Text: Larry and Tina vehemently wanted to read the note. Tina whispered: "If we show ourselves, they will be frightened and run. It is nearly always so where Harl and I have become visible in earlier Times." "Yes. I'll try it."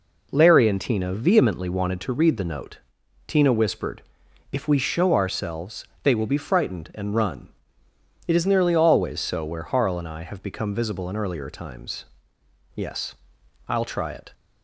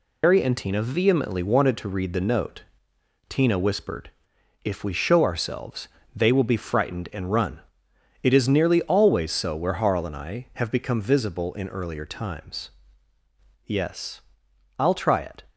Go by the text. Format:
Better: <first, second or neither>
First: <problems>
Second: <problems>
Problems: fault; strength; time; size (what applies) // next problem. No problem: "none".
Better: first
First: none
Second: loses the start of "Larry"; at 0.2 s; 150 ms